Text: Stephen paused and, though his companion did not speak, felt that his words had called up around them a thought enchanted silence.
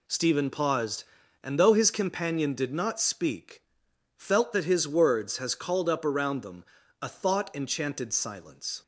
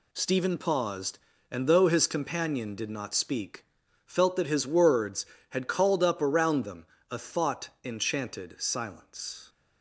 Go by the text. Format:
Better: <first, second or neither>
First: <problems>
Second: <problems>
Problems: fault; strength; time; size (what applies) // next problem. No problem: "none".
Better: second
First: says "has" for "had"; at 5.3 s // pauses between "them" and "a"; at 6.6 s; 0.38 s long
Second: pauses between "them" and "a"; slight; at 6.8 s; 0.24 s long